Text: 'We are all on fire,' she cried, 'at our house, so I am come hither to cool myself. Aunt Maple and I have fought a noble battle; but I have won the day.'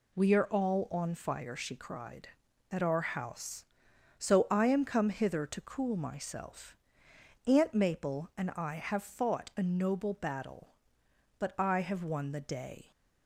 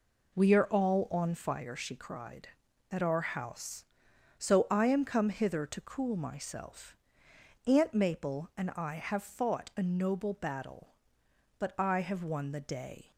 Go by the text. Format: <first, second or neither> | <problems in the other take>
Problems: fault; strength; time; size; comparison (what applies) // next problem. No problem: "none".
first | starts louder than the rest; noticeable; until 1.6 s; 4 dB